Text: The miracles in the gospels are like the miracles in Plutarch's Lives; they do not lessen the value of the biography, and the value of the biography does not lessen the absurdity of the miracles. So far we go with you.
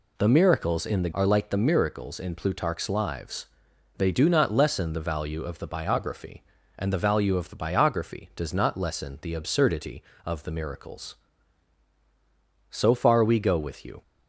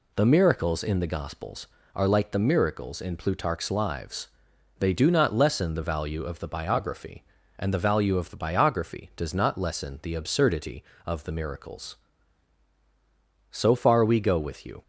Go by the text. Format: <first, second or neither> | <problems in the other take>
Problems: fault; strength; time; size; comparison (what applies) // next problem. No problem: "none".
second | skips "gospels"; at 1.1 s